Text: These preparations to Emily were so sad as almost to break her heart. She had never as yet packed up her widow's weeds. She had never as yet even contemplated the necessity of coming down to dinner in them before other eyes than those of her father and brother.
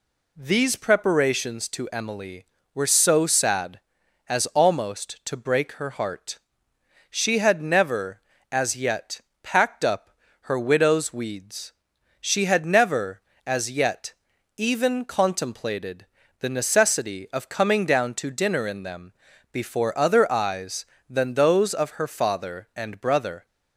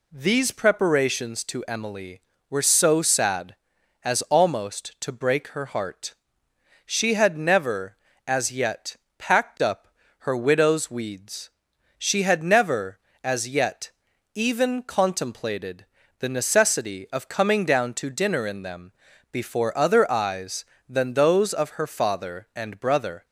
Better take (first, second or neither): neither